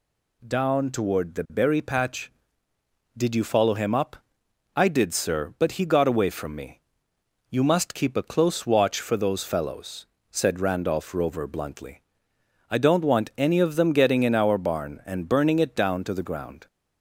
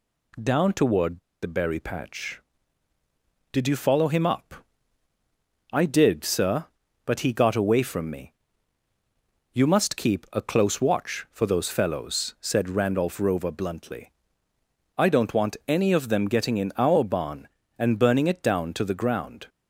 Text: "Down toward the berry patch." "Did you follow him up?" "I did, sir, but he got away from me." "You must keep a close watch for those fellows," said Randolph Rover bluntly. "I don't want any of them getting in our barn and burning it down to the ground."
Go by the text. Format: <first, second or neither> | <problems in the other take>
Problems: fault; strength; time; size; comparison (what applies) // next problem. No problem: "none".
first | pauses between "toward" and "the"; slight; at 1.1 s; 0.24 s long